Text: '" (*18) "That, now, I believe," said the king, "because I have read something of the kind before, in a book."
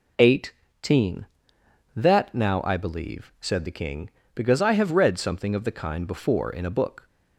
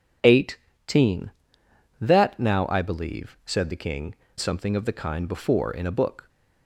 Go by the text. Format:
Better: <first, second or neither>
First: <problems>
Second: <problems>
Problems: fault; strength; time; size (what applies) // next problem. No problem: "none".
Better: first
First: none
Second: starts louder than the rest; until 1.2 s; 6.5 dB // skips "because I have read"; at 4.2 s